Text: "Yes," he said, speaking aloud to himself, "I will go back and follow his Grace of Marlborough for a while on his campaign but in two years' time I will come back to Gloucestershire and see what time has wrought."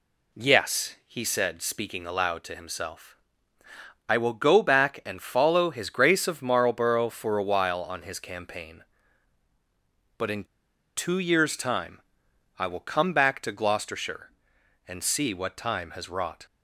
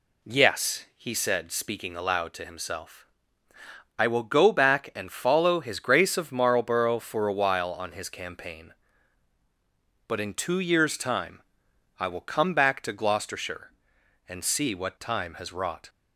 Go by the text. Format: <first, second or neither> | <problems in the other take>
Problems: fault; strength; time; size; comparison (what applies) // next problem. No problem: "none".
second | pauses between "in" and "two"; noticeable; at 10.4 s; 0.51 s long // pauses between "time" and "I"; noticeable; at 11.9 s; 0.60 s long; noticeable in the second